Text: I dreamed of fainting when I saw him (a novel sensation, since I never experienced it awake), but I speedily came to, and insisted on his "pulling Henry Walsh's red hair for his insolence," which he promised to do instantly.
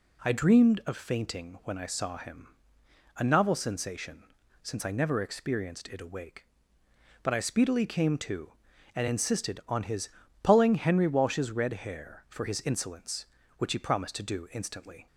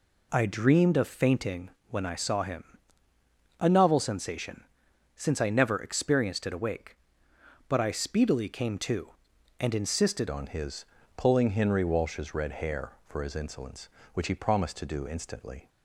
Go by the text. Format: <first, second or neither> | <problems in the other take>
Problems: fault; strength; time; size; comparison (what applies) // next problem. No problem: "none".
first | pauses between "fainting" and "when"; slight; at 1.7 s; 0.18 s long // changes voice at "on"; from 10.3 s on; 5.3 s long // pauses between "his" and "pulling"; slight; at 10.8 s; 0.30 s long; slight in the first